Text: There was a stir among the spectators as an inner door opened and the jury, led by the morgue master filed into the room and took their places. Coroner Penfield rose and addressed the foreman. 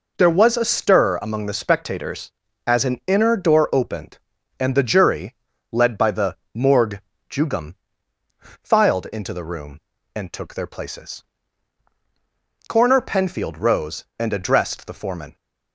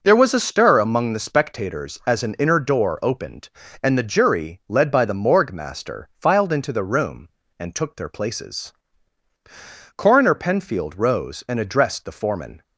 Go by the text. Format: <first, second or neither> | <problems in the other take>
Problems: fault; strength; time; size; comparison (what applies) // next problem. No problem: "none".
second | pauses between "the" and "morgue"; slight; at 6.3 s; 0.16 s long // says "jugum" for "master"; at 7.2 s